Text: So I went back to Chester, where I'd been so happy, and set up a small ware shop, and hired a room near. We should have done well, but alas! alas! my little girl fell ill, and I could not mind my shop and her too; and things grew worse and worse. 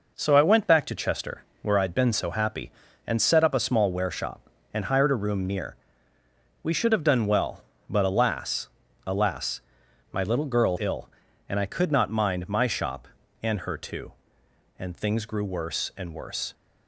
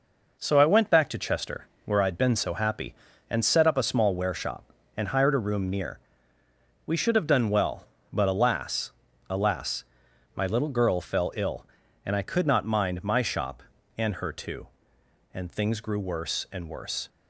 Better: second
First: skips "fell"; at 10.7 s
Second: none

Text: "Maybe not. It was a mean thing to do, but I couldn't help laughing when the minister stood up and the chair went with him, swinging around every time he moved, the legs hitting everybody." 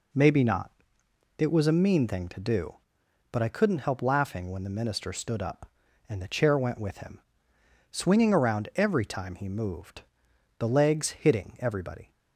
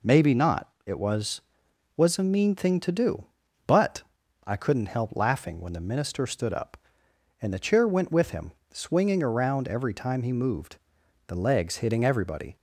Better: first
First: none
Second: says "was" twice; at 1.9 s // pauses between "but" and "I"; at 4.0 s; 0.44 s long

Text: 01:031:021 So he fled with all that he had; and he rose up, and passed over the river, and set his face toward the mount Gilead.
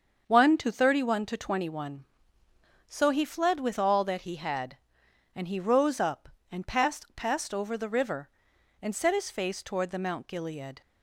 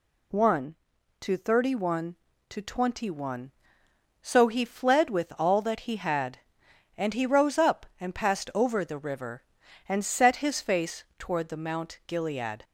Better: second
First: starts louder than the rest; until 1.2 s; 6.5 dB // says "passed" twice; at 7.1 s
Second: none

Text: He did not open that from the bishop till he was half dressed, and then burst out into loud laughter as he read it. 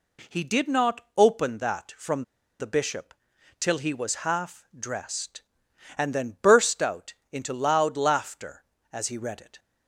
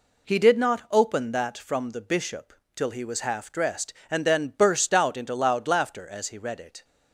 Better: second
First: pauses between "from" and "the"; slight; at 2.2 s; 0.36 s long // pauses between "bishop" and "till"; noticeable; at 3.1 s; 0.46 s long // pauses between "out" and "into"; slight; at 7.1 s; 0.20 s long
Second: pauses between "bishop" and "till"; slight; at 2.5 s; 0.22 s long

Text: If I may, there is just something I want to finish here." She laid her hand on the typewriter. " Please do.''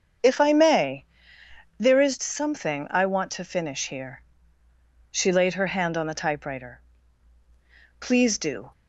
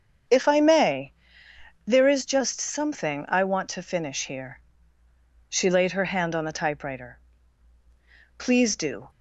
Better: second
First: starts louder than the rest; strong; until 1.9 s; 7.5 dB // skips "just"; at 2.1 s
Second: starts louder than the rest; strong; until 2.0 s; 7.5 dB

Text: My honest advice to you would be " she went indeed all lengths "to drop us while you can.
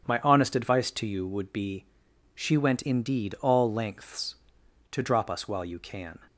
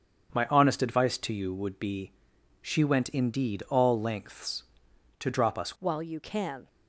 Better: first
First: none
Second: changes voice at "while"; from 5.7 s on; 0.9 s long

